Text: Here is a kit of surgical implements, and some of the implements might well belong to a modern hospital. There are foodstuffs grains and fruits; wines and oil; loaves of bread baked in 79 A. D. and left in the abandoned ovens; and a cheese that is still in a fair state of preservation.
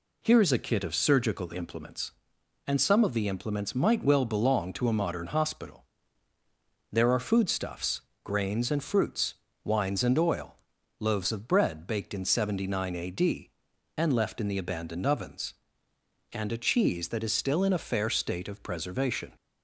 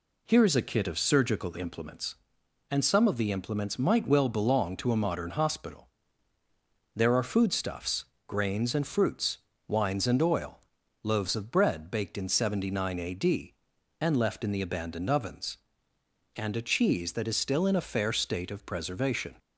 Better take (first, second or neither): neither